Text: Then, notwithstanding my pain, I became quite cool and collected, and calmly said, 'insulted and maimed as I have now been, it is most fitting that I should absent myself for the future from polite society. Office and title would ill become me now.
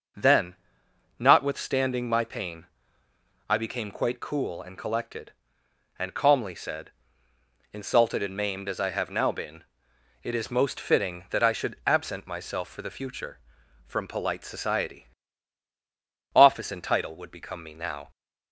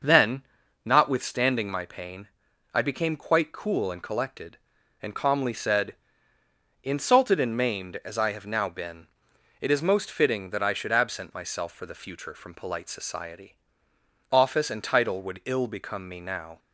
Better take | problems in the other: second | skips "ill"; at 17.3 s

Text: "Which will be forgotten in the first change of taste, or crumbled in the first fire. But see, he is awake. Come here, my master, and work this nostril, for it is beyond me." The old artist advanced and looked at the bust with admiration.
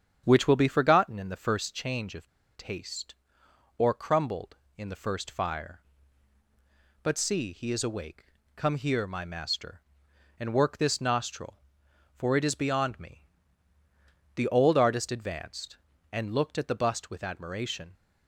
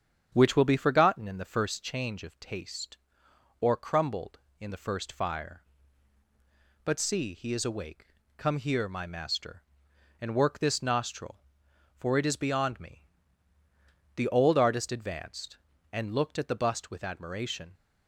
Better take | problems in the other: second | starts louder than the rest; strong; until 1.2 s; 8.5 dB; strong in the second // pauses between "of" and "taste"; slight; at 2.2 s; 0.28 s long

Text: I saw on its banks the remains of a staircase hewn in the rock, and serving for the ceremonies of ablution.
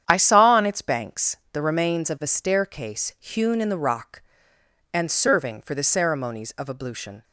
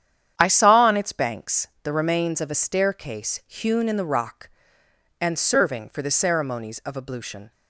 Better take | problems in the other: neither | starts louder than the rest; strong; the same in both // pauses between "banks" and "the"; slight; the same in both

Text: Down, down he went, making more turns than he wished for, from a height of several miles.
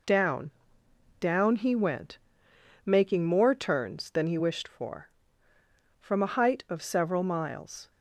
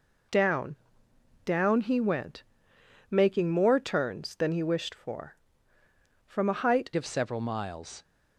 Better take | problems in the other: first | changes voice at "of"; from 6.9 s on; 1.1 s long

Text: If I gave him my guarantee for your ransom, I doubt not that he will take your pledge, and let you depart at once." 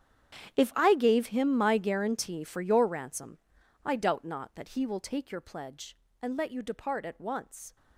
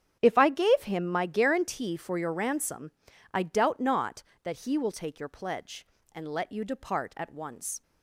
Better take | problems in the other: second | gets quieter; strong; throughout; 18.5 dB // starts louder than the rest; strong; until 1.6 s; 10 dB; strong in the second

